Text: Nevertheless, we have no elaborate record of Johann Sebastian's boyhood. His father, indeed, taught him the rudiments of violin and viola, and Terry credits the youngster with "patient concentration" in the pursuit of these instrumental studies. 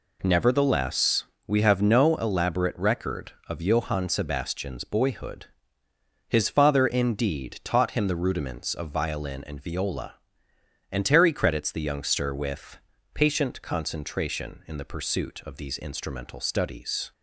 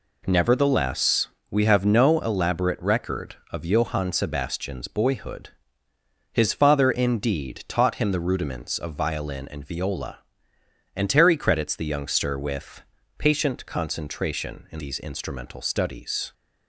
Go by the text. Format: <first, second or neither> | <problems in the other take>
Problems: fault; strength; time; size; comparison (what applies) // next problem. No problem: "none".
first | pauses between "with" and "patient"; slight; at 12.8 s; 0.36 s long; slight in the first // skips "the pursuit of"; at 14.7 s